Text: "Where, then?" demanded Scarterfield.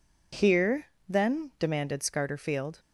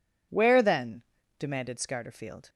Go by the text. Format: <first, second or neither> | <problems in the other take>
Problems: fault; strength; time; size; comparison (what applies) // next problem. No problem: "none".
second | says "Here" for "Where"; at 0.3 s